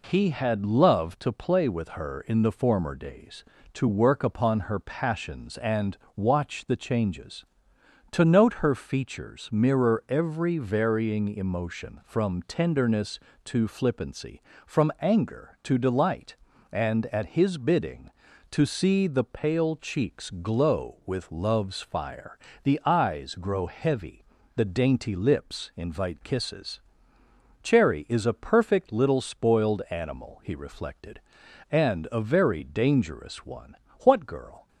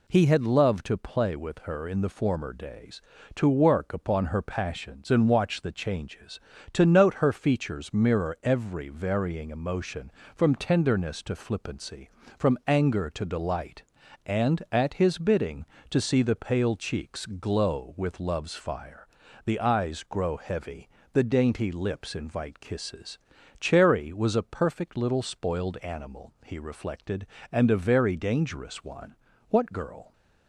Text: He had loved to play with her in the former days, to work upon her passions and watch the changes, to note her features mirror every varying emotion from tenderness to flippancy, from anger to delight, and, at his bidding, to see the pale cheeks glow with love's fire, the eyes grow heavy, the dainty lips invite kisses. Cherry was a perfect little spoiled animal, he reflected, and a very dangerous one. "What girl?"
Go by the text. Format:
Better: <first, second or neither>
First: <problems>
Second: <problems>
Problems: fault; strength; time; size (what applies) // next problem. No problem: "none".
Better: second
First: pauses between "and" and "watch"; slight; at 5.9 s; 0.20 s long // says "is" for "was"; at 28.0 s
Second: none